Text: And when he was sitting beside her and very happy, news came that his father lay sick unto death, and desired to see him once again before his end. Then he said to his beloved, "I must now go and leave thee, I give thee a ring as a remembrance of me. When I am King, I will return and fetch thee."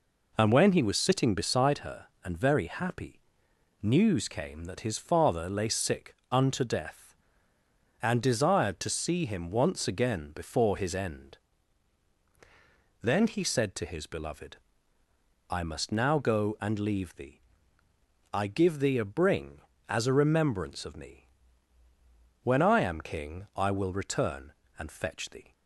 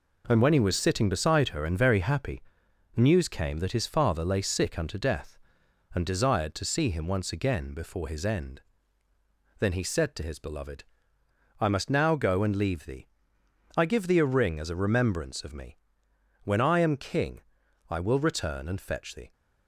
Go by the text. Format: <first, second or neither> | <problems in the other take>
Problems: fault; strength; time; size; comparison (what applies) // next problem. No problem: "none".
second | pauses between "sick" and "unto"; slight; at 6.1 s; 0.18 s long // says "bring" for "ring"; at 19.0 s